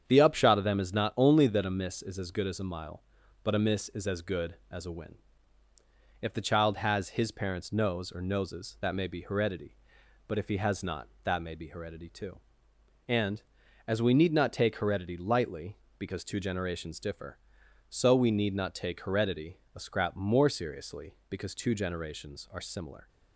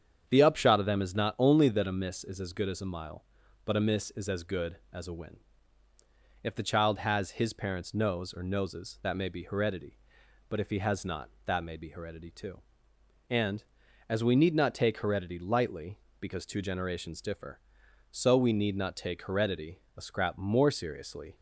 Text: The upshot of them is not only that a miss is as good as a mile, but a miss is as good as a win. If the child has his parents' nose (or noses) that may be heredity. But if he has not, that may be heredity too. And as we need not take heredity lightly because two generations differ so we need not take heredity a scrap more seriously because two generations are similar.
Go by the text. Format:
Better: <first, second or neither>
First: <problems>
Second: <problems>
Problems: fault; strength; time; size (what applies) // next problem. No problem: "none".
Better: first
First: starts louder than the rest; strong; until 1.0 s; 8 dB // pauses between "heredity" and "a"; slight; at 19.5 s; 0.18 s long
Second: starts louder than the rest; strong; until 1.3 s; 8 dB // pauses between "heredity" and "a"; slight; at 19.7 s; 0.18 s long // stops before "because two generations are similar"; at 21.3 s